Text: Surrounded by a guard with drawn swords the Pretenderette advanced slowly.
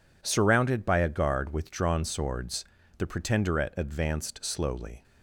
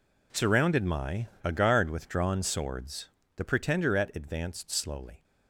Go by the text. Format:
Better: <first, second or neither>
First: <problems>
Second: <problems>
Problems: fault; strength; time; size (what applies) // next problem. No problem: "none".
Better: first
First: pauses between "swords" and "the"; slight; at 2.6 s; 0.36 s long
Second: says "my" for "by"; at 0.8 s // pauses between "swords" and "the"; slight; at 3.0 s; 0.26 s long